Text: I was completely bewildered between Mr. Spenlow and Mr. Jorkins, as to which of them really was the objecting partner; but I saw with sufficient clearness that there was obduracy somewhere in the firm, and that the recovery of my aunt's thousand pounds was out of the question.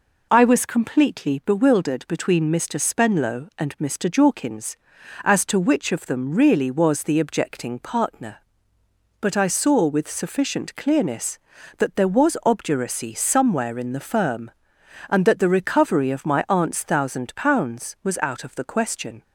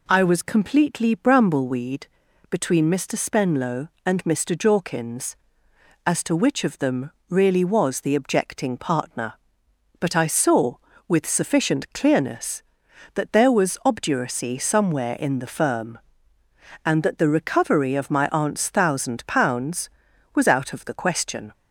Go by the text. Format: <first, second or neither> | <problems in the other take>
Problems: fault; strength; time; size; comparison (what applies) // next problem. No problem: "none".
first | says "brambleweed" for "bewildered"; at 1.1 s // pauses between "them" and "really"; slight; at 7.1 s; 0.18 s long